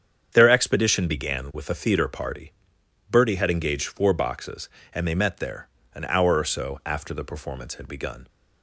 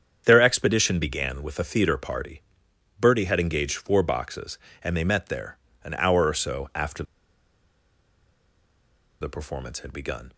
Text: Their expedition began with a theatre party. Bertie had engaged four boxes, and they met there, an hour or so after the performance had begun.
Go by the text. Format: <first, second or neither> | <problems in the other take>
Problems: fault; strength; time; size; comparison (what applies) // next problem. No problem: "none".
first | starts louder than the rest; strong; until 1.2 s; 8 dB; strong in the first // pauses between "after" and "the"; strong; at 7.0 s; 2.1 s long